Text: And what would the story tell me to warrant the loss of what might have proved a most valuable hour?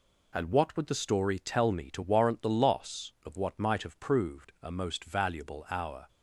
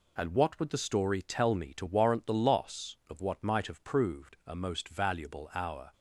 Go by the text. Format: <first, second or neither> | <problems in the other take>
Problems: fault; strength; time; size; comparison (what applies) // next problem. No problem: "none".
neither | none